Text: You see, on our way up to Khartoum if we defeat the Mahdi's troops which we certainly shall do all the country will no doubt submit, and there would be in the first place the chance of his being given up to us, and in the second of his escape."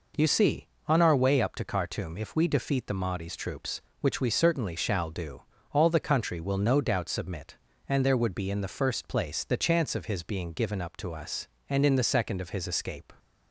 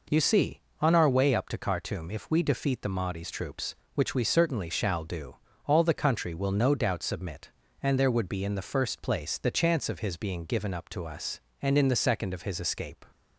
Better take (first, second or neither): neither